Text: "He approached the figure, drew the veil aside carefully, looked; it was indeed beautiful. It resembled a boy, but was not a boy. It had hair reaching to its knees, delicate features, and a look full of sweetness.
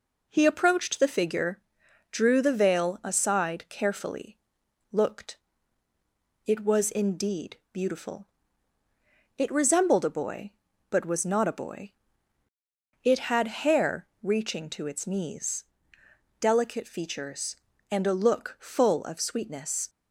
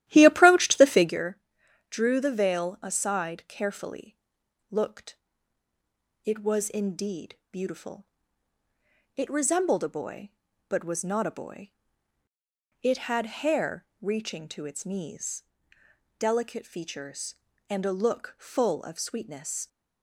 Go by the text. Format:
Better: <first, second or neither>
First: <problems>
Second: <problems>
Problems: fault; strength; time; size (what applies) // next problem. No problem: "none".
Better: first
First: pauses between "indeed" and "beautiful"; slight; at 7.5 s; 0.16 s long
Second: starts louder than the rest; strong; until 1.2 s; 13.5 dB // pauses between "indeed" and "beautiful"; slight; at 7.3 s; 0.16 s long